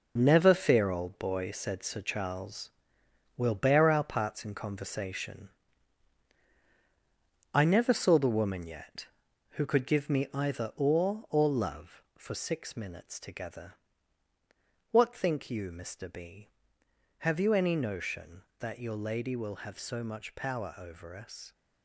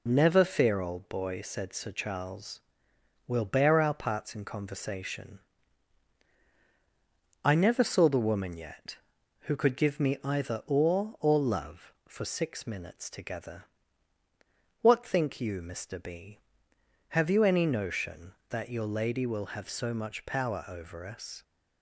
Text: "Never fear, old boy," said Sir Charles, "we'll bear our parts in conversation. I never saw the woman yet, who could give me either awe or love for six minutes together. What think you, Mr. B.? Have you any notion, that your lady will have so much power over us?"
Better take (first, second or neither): second